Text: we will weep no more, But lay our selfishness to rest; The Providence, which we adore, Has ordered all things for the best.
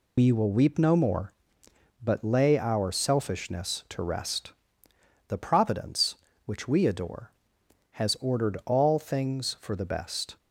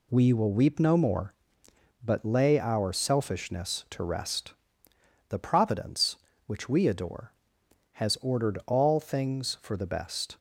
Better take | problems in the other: second | loses the start of "we"; at 0.1 s; 90 ms

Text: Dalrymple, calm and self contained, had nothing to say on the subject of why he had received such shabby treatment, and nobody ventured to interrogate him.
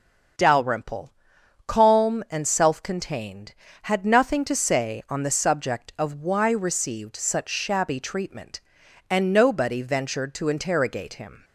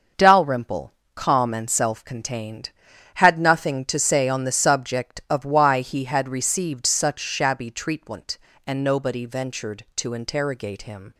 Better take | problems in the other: second | starts louder than the rest; until 1.9 s; 6.5 dB; also in the second // skips "he had"; at 6.5 s

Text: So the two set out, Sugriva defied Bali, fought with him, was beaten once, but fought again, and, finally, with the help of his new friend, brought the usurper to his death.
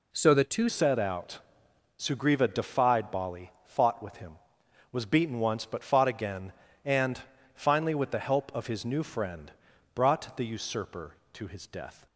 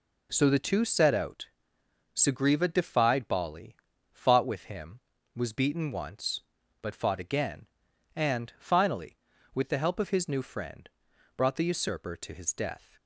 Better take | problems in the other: second | changes voice at "set"; from 0.6 s on; 11.4 s long

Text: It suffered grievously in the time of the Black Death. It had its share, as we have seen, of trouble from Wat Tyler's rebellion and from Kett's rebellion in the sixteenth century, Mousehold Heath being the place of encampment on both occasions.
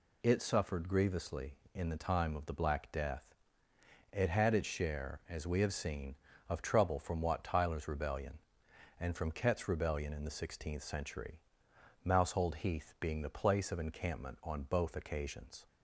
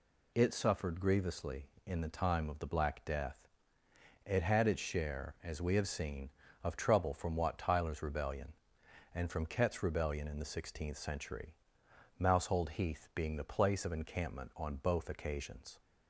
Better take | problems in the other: neither | none

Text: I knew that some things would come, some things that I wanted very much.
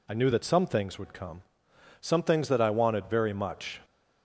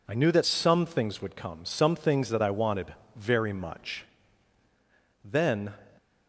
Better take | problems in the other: first | pauses between "wanted" and "very"; slight; at 2.9 s; 0.22 s long // goes on to say "Then"; from 5.2 s on; 0.50 s long

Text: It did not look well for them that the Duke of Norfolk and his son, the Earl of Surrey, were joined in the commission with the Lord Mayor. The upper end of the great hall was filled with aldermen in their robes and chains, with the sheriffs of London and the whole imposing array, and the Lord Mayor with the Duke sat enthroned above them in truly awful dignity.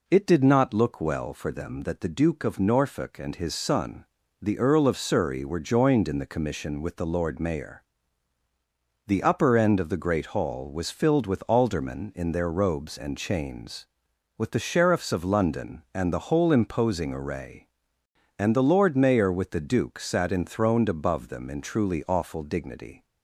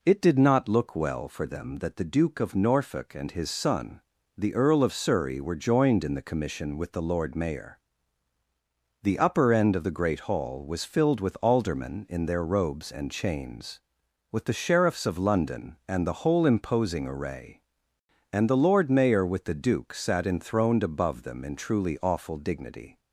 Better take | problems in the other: neither | none

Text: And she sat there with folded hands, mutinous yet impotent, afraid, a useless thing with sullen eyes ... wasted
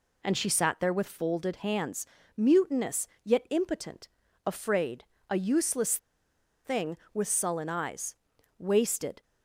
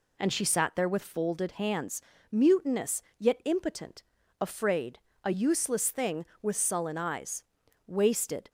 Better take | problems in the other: second | pauses between "mutinous" and "yet"; slight; at 3.0 s; 0.18 s long; slight in the second // pauses between "useless" and "thing"; noticeable; at 5.9 s; 0.68 s long

